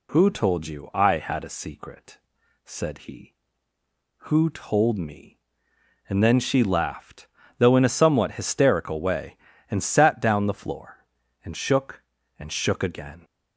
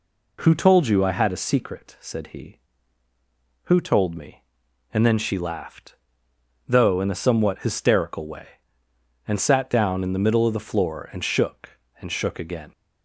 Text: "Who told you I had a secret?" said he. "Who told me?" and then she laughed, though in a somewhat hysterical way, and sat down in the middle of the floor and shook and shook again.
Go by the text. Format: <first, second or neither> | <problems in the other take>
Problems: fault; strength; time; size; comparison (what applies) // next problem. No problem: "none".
second | skips "in the middle of"; at 10.4 s